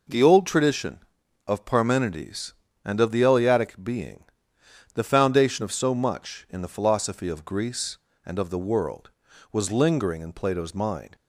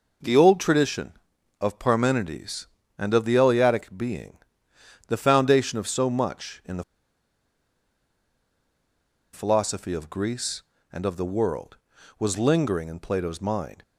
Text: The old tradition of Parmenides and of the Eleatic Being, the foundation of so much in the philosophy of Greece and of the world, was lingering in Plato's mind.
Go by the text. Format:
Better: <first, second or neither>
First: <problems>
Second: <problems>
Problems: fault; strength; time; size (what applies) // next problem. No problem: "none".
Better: first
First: none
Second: pauses between "the" and "philosophy"; strong; at 6.8 s; 2.4 s long